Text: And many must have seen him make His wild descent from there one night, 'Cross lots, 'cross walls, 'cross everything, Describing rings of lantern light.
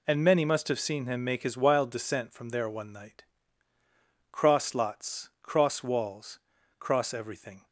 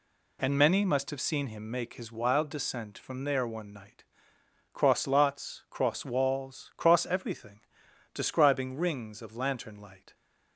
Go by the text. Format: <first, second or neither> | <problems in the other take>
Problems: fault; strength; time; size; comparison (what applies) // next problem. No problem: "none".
second | stops before "Describing rings of lantern light"; at 7.6 s